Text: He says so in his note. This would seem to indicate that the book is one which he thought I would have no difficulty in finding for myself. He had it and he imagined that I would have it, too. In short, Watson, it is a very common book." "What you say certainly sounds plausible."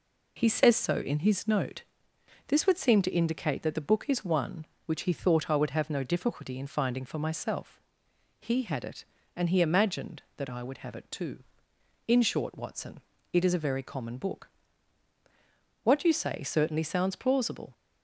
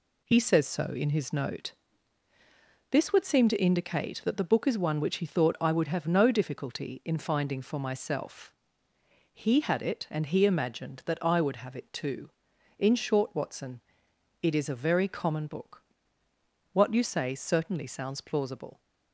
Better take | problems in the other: neither | none

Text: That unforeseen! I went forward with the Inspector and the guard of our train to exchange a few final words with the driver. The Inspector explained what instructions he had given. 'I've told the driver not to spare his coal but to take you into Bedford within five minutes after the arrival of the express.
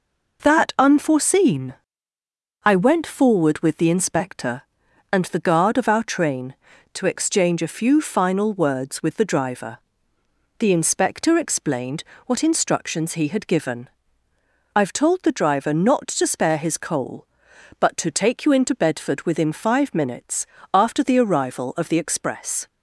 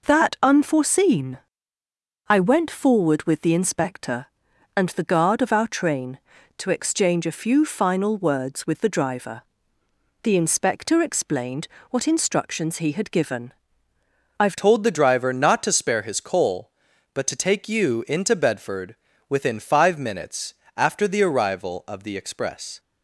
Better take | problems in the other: first | pauses between "explained" and "what"; slight; at 11.6 s; 0.20 s long; slight in the first // changes voice at "told"; from 14.5 s on; 8.2 s long // pauses between "Bedford" and "within"; slight; at 18.9 s; 0.32 s long // pauses between "minutes" and "after"; slight; at 20.5 s; 0.24 s long; slight in the first

